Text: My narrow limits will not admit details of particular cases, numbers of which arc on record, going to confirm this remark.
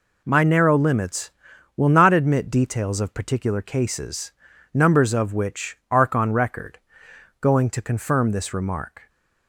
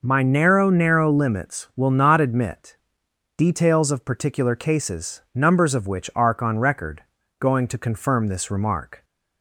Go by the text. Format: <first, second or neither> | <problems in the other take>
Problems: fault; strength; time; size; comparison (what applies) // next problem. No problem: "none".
first | says "narrow" twice; at 0.6 s // pauses between "admit" and "details"; noticeable; at 2.7 s; 0.62 s long